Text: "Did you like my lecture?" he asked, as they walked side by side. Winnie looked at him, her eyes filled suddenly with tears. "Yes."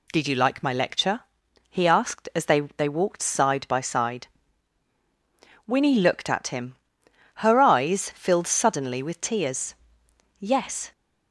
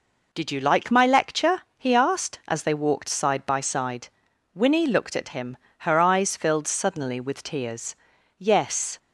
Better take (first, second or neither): second